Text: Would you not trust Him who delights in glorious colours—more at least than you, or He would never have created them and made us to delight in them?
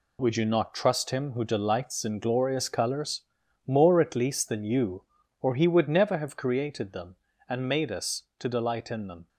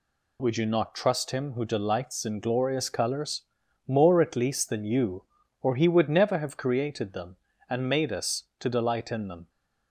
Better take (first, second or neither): second